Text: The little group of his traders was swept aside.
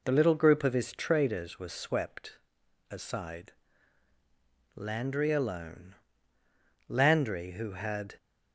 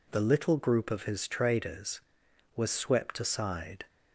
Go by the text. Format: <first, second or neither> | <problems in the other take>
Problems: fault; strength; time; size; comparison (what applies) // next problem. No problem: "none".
second | pauses between "swept" and "aside"; noticeable; at 2.3 s; 0.54 s long // goes on to say "Landry alone Landry who had"; strong; from 4.7 s on; 3.4 s long